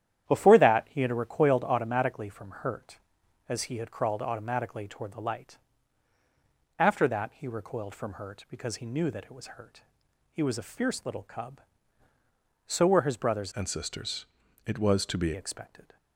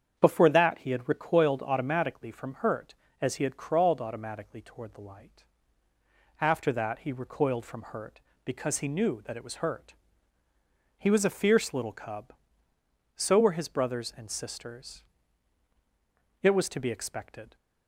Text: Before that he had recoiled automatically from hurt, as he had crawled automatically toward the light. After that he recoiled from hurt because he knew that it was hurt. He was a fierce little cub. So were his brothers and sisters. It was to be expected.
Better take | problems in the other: second | starts louder than the rest; strong; until 1.3 s; 10.5 dB; strong in the second // changes voice from "and" to "be"; from 13.5 to 15.3 s; 1.8 s long

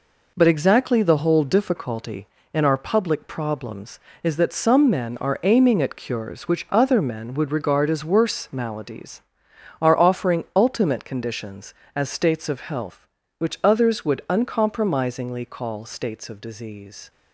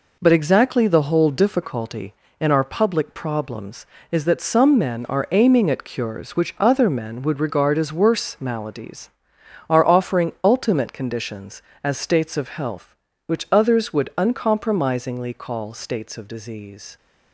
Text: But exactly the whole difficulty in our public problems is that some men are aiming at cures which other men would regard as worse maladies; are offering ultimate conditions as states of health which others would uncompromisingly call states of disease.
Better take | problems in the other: neither | none

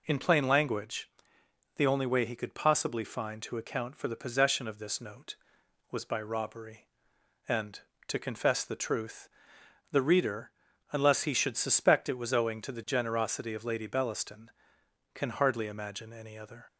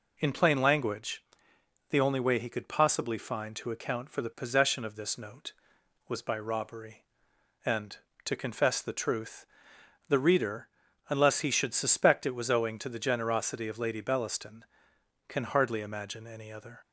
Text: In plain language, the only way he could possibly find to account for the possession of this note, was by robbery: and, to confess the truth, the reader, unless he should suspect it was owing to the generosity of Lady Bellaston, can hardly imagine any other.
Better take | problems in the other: neither | none

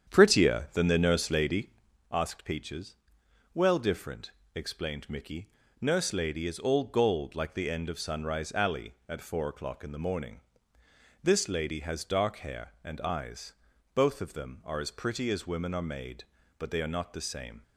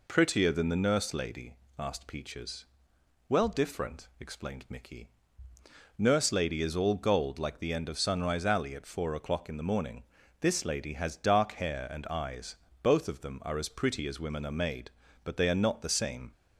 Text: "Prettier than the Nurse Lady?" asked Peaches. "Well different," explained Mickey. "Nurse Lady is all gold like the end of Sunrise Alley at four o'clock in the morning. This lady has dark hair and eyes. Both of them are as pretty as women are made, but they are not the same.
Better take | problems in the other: second | starts louder than the rest; strong; until 1.9 s; 8.5 dB

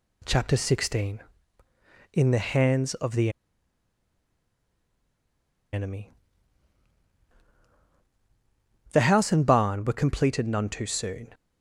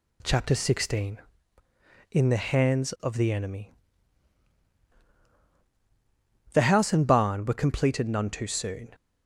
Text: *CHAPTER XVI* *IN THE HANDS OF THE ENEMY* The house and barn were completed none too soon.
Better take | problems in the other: second | pauses between "THE" and "ENEMY"; strong; at 3.2 s; 2.4 s long // pauses between "ENEMY" and "The"; strong; at 6.1 s; 2.7 s long; strong in the second

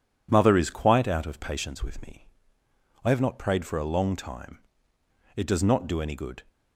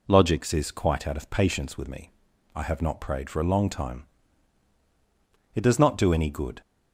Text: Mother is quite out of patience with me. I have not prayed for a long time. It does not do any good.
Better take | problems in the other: first | says "Logics" for "Mother"; at 0.0 s

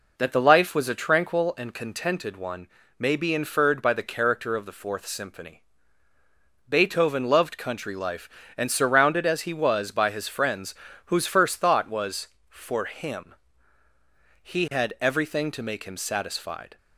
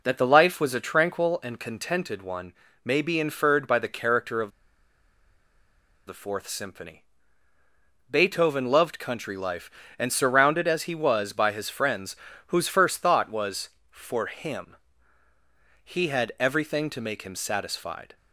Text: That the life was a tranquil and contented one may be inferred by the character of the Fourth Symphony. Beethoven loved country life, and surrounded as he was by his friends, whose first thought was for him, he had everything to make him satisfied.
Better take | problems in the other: first | pauses between "one" and "may"; slight; at 2.5 s; 0.30 s long; slight in the first // pauses between "of" and "the"; strong; at 4.5 s; 1.5 s long

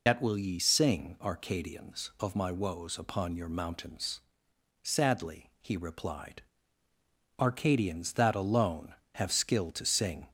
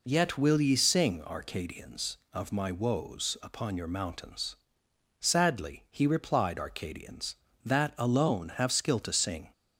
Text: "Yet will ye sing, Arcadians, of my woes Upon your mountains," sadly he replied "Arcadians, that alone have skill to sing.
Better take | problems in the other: second | loses the start of "Yet"; at 0.0 s; 120 ms // pauses between "replied" and "Arcadians"; noticeable; at 6.4 s; 0.98 s long

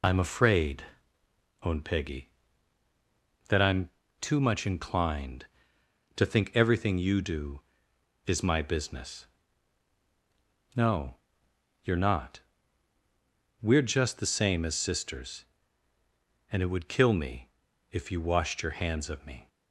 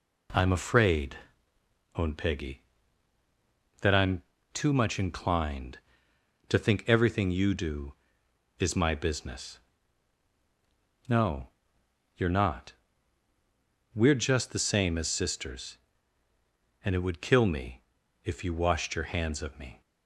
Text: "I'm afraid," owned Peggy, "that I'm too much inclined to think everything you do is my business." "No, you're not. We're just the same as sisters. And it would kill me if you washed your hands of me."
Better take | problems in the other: second | loses the start of "I'm"; at 0.0 s; 65 ms // pauses between "I'm" and "too"; slight; at 3.9 s; 0.30 s long; slight in the second // pauses between "me" and "if"; at 17.4 s; 0.42 s long; also in the second

